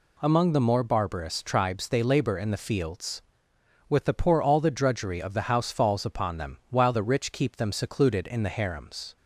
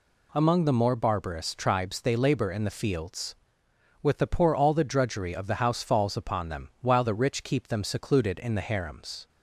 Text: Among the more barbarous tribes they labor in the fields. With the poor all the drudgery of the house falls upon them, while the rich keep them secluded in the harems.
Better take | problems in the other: neither | none

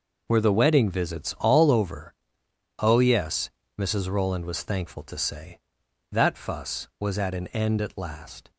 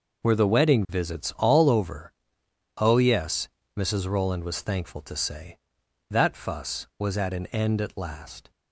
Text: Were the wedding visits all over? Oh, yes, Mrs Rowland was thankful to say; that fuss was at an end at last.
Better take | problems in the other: neither | none

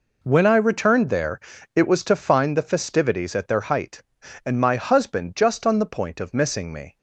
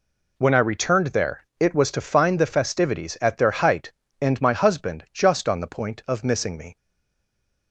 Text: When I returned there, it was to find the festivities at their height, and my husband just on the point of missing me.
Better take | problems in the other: first | stays silent after the last word; slight; from 6.7 s on; 1.0 s long

